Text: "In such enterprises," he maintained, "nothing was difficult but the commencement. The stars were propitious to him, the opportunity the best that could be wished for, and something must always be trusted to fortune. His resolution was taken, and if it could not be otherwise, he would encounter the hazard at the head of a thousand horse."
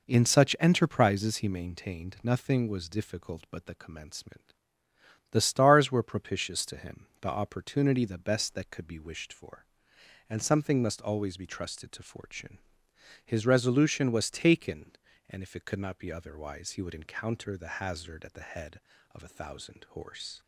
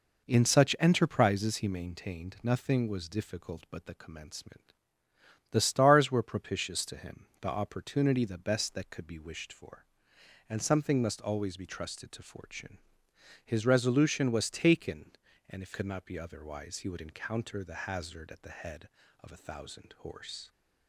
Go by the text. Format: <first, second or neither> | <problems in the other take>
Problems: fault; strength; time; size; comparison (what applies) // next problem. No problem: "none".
first | skips "it"; at 15.7 s